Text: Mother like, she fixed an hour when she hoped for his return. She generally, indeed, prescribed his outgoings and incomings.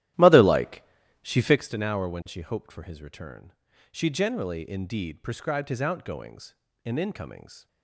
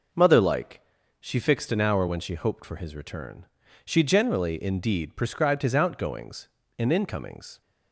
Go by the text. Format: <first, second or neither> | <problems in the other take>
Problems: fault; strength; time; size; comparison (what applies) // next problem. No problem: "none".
second | starts louder than the rest; strong; until 1.6 s; 13.5 dB